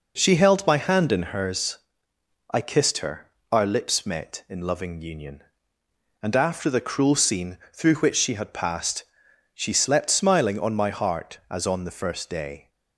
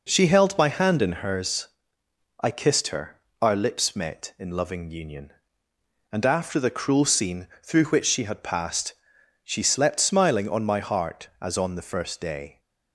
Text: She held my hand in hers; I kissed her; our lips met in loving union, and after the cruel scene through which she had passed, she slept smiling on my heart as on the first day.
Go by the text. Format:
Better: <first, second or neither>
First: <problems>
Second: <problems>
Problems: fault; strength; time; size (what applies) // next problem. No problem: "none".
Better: neither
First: pauses between "scene" and "through"; slight; at 7.5 s; 0.16 s long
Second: pauses between "scene" and "through"; slight; at 7.4 s; 0.16 s long